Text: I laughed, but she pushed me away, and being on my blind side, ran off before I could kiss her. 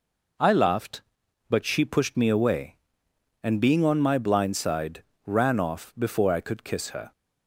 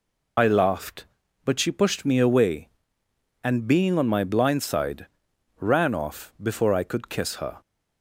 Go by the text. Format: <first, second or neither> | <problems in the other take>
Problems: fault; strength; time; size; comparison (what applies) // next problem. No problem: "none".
first | loses the start of "I"; at 0.3 s; 50 ms